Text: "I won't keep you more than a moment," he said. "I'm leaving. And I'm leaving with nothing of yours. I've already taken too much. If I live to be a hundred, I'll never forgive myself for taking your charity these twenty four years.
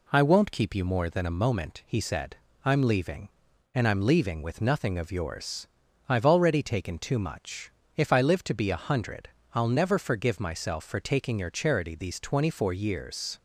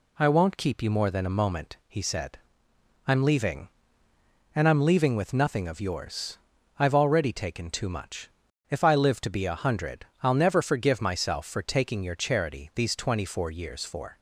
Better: first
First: none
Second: goes on to say "For"; slight; from 13.8 s on; 0.34 s long

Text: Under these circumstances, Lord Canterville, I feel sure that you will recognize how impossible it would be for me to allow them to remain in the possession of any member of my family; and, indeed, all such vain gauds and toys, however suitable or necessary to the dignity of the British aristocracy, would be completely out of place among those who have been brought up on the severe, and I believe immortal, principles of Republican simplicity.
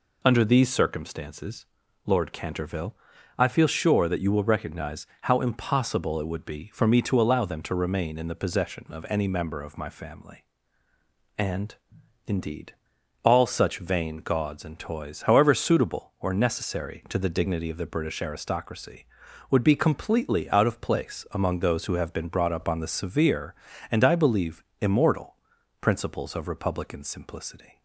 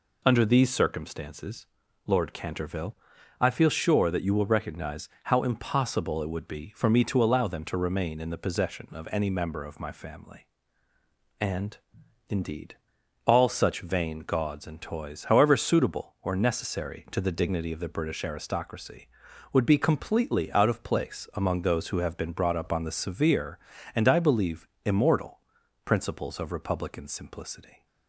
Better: neither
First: pauses between "recognize" and "how"; slight; at 5.0 s; 0.16 s long // pauses between "believe" and "immortal"; slight; at 24.6 s; 0.16 s long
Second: pauses between "recognize" and "how"; slight; at 5.0 s; 0.16 s long // pauses between "believe" and "immortal"; slight; at 24.6 s; 0.16 s long

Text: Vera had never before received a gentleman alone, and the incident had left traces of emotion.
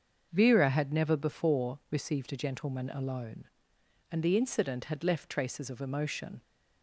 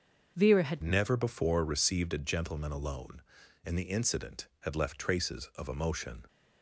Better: first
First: starts louder than the rest; until 1.3 s; 6.5 dB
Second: starts louder than the rest; until 1.3 s; 6.5 dB // changes voice at "never"; from 0.8 s on; 5.4 s long

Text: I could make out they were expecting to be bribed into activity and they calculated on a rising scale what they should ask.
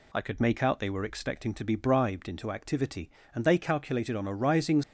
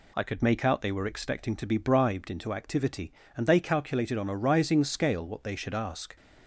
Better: second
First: stops before "scale what they should ask"; at 4.8 s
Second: none

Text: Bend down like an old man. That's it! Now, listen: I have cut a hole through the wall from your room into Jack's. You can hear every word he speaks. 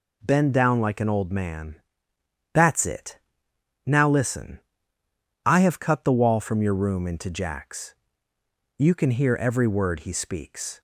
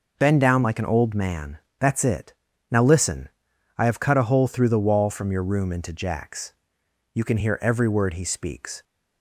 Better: second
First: skips "a hole through"; at 6.0 s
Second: none

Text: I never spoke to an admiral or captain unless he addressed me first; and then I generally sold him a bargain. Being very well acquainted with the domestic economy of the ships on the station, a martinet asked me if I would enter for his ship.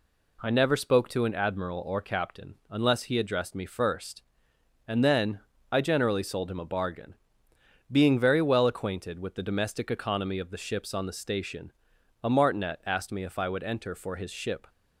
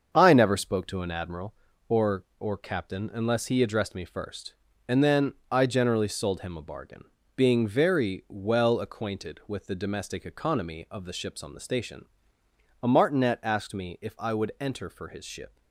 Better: first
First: pauses between "then" and "I"; slight; at 5.4 s; 0.28 s long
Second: starts louder than the rest; until 1.1 s; 6.5 dB // says "or" twice; at 2.3 s // pauses between "then" and "I"; slight; at 5.3 s; 0.18 s long

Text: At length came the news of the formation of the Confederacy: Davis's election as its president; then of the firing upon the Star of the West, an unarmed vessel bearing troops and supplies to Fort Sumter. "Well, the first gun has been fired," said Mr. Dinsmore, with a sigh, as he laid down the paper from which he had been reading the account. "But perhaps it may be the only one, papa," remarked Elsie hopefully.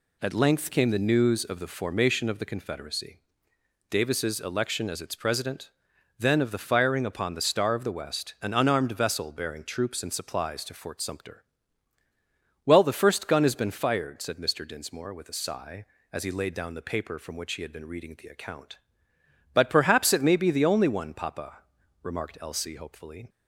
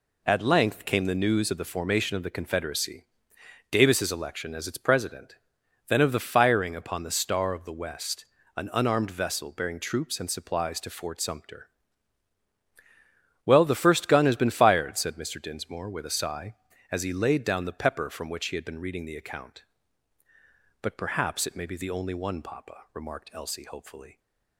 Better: first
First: none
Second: says "pepper" for "paper"; at 17.8 s

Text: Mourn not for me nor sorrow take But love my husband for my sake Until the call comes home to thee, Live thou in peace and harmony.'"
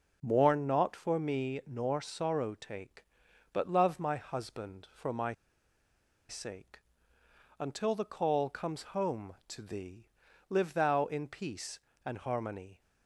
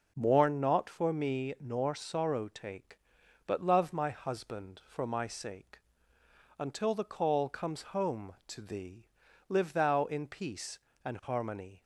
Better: second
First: pauses between "my" and "sake"; noticeable; at 5.3 s; 0.97 s long // pauses between "sake" and "Until"; noticeable; at 6.8 s; 0.80 s long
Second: pauses between "sake" and "Until"; noticeable; at 5.7 s; 0.80 s long

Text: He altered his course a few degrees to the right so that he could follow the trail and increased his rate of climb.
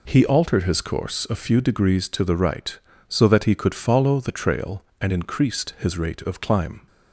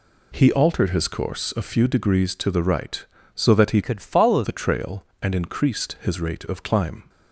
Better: first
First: none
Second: changes voice from "could" to "follow"; from 3.8 to 4.4 s; 0.6 s long

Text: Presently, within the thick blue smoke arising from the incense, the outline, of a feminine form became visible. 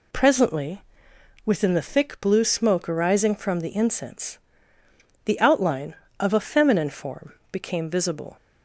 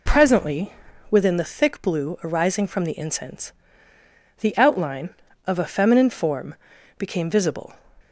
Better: first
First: pauses between "form" and "became"; slight; at 7.3 s; 0.16 s long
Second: skips "smoke"; at 2.1 s // pauses between "form" and "became"; at 6.5 s; 0.42 s long

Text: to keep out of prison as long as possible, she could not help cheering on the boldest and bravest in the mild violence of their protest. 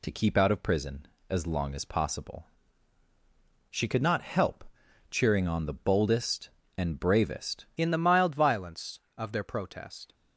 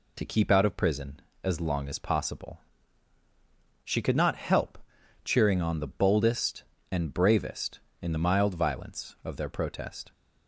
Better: second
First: pauses between "help" and "cheering"; noticeable; at 4.6 s; 0.46 s long // changes voice at "in"; from 7.7 s on; 2.4 s long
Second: pauses between "help" and "cheering"; noticeable; at 4.7 s; 0.46 s long

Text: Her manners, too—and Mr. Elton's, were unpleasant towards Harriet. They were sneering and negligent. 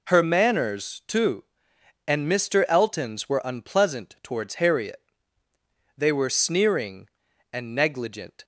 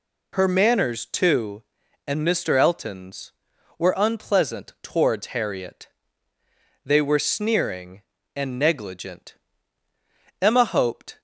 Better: first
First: none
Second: goes on to say "Emma hoped"; noticeable; from 10.4 s on; 0.78 s long

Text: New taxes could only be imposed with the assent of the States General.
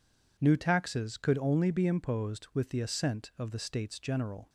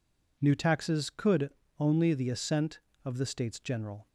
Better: first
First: none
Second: pauses between "could" and "only"; slight; at 1.4 s; 0.30 s long // skips "be imposed with"; at 2.1 s

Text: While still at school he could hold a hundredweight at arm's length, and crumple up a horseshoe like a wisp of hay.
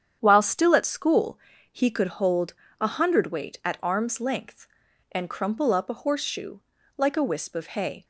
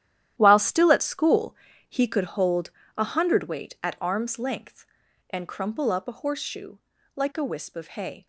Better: first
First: starts louder than the rest; strong; until 1.2 s; 8.5 dB // pauses between "school" and "he"; slight; at 1.3 s; 0.34 s long // pauses between "hold" and "a"; slight; at 2.5 s; 0.26 s long // pauses between "horseshoe" and "like"; at 6.5 s; 0.38 s long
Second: gets quieter; strong; throughout; 12.5 dB // starts louder than the rest; strong; until 1.3 s; 11.5 dB // pauses between "school" and "he"; slight; at 1.5 s; 0.34 s long // pauses between "hold" and "a"; slight; at 2.6 s; 0.26 s long // pauses between "horseshoe" and "like"; at 6.7 s; 0.38 s long

